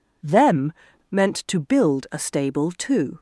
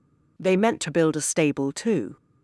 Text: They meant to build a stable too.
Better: second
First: says "Them" for "They"; at 0.2 s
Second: none

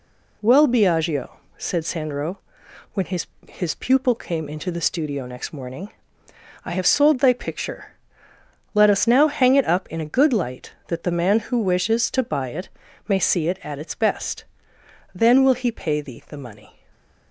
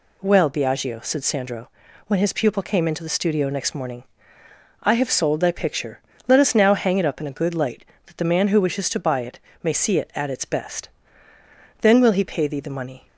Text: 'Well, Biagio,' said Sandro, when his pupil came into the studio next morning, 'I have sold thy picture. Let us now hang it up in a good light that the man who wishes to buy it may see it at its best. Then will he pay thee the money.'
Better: second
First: says "his" twice; at 3.4 s // pauses between "it" and "may"; at 12.6 s; 0.40 s long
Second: pauses between "it" and "may"; slight; at 9.3 s; 0.24 s long

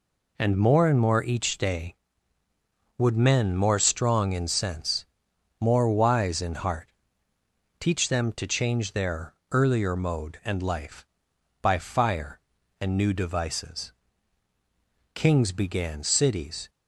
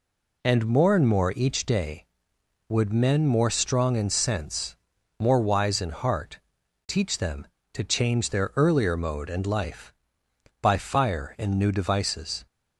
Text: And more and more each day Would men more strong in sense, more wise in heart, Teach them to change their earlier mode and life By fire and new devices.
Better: second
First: pauses between "their" and "earlier"; slight; at 9.3 s; 0.20 s long // goes on to say "Kings began Cities"; from 15.1 s on; 1.5 s long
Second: none

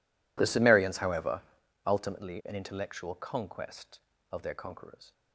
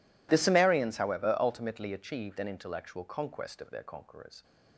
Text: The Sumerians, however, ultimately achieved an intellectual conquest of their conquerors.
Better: second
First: skips "achieved"; at 2.4 s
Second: none

